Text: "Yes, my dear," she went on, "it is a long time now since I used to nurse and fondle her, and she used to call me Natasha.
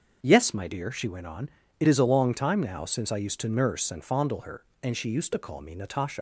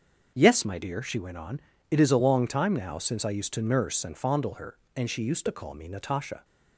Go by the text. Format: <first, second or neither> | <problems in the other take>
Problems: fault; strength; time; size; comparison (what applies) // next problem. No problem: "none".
second | starts louder than the rest; until 1.2 s; 6.5 dB; also in the second // leaves "Natasha" unfinished; at 6.1 s; 105 ms